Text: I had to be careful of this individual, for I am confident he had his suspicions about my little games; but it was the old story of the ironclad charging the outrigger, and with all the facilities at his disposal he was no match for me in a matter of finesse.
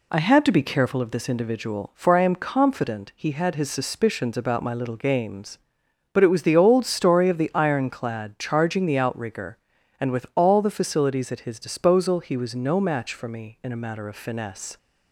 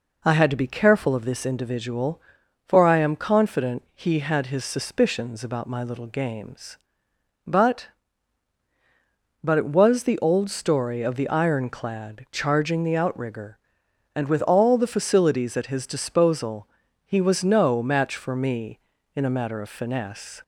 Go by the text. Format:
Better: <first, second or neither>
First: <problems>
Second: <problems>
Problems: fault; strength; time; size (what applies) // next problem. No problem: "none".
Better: first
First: none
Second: says "but" twice; at 9.4 s // pauses between "disposal" and "he"; slight; at 16.6 s; 0.36 s long